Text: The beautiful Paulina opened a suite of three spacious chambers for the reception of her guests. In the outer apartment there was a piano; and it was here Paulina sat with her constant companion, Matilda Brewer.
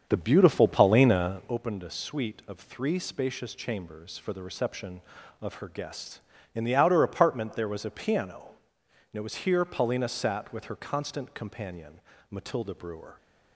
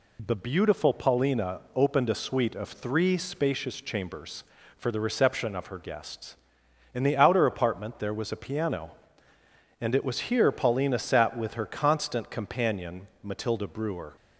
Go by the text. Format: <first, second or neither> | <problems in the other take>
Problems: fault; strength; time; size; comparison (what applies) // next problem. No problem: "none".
second | starts louder than the rest; until 1.6 s; 7 dB